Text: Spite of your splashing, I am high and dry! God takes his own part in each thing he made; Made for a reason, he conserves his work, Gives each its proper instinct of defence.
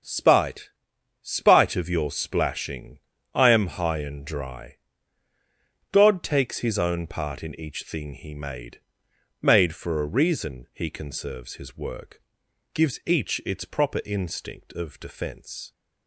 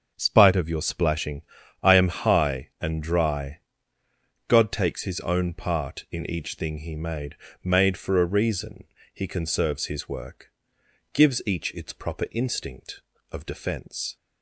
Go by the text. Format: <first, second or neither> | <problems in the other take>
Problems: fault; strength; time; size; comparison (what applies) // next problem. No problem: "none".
second | starts louder than the rest; until 1.5 s; 7 dB; also in the second // says "Spite" twice; at 1.2 s